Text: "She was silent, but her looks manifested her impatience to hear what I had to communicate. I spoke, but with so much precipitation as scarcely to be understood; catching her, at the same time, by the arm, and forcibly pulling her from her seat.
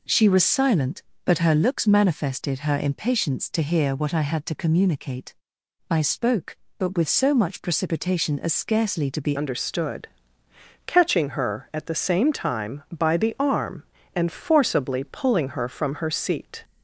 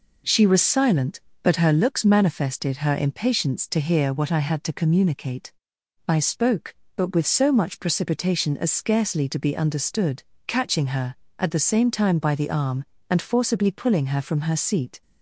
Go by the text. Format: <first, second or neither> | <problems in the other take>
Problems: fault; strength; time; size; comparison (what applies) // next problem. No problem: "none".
second | changes voice at "understood"; from 9.3 s on; 7.3 s long